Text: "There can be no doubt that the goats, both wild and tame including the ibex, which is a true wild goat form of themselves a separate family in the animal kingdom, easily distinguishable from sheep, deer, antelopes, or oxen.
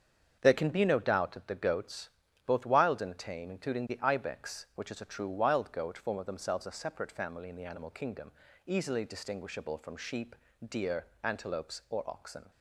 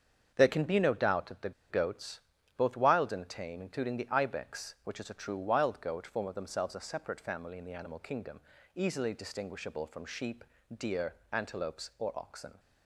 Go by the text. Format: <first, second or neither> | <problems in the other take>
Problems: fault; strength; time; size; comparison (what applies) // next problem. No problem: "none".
first | starts louder than the rest; strong; until 1.3 s; 7 dB; strong in the first // pauses between "the" and "goats"; slight; at 1.5 s; 0.19 s long